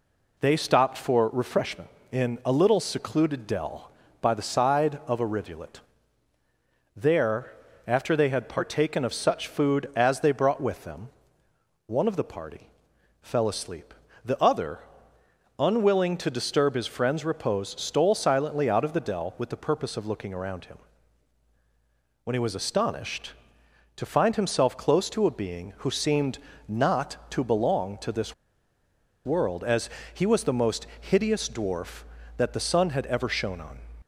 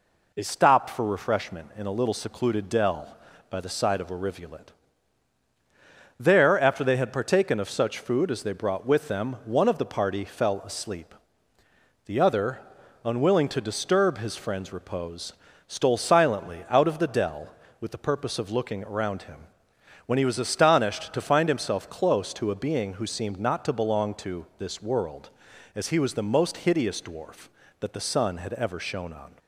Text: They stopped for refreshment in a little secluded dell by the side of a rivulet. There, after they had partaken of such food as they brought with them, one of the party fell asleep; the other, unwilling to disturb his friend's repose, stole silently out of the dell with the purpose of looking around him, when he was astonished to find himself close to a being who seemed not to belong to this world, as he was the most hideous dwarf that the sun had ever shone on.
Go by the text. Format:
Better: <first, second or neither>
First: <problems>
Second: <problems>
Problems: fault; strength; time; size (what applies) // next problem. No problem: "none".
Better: second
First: pauses between "party" and "fell"; noticeable; at 12.6 s; 0.52 s long // pauses between "seemed" and "not"; slight; at 26.3 s; 0.30 s long // pauses between "this" and "world"; noticeable; at 28.3 s; 0.91 s long // pauses between "as" and "he"; slight; at 29.9 s; 0.24 s long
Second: none